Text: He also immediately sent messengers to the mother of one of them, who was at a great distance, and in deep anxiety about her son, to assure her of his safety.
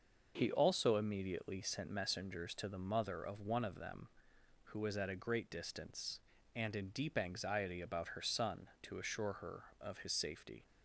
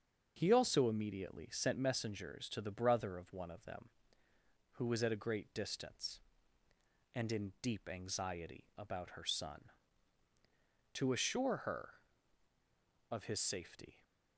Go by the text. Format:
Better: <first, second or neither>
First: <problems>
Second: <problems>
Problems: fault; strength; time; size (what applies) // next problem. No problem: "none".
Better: first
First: starts louder than the rest; noticeable; until 1.3 s; 6 dB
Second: starts louder than the rest; until 1.3 s; 6.5 dB // says "brother" for "mother"; at 2.6 s